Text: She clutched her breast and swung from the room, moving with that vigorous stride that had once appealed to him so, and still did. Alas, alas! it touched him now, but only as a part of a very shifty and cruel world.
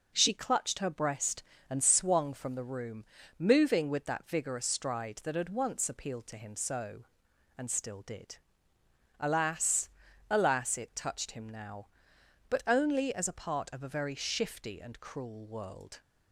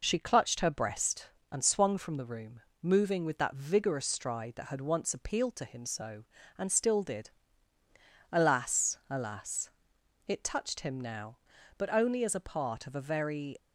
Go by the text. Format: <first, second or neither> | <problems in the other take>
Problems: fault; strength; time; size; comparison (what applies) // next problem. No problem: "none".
first | stops before "shifty and cruel world"; at 13.5 s